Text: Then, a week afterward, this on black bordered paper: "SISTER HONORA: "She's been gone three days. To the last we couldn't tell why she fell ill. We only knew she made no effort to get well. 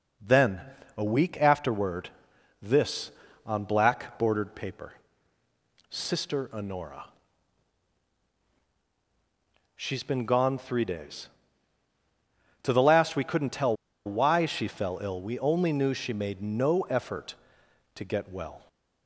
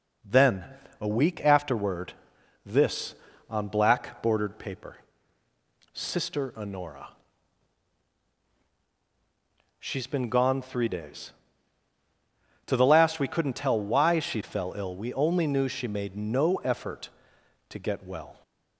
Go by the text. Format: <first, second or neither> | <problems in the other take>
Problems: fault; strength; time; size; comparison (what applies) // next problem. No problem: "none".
second | pauses between "tell" and "why"; slight; at 13.7 s; 0.32 s long